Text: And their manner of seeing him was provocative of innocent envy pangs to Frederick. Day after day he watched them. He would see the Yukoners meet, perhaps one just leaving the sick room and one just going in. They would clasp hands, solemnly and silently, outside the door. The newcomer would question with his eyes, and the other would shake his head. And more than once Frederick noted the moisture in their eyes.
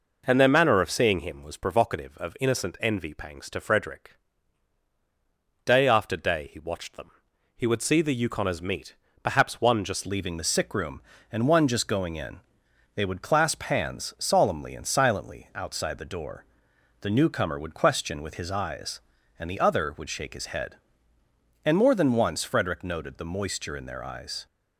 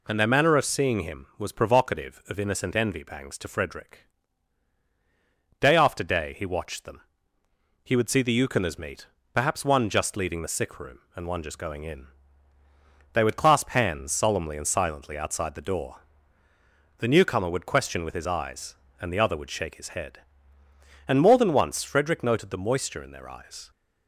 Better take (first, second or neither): second